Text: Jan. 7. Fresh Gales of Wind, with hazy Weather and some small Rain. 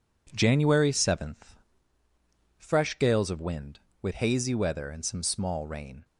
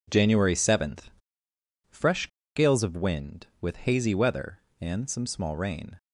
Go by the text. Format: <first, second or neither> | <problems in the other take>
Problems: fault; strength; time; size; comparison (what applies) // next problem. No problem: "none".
first | pauses between "Fresh" and "Gales"; slight; at 2.2 s; 0.27 s long